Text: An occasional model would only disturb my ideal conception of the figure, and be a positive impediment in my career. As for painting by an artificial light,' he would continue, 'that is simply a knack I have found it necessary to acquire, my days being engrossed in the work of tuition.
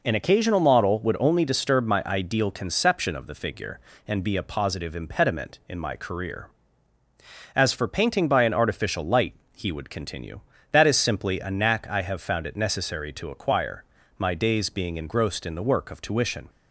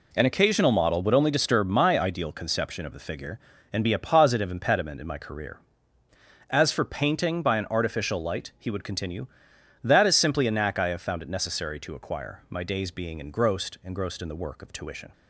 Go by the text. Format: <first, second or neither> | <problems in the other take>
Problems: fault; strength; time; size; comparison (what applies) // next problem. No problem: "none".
first | says "engrossed" twice; at 13.8 s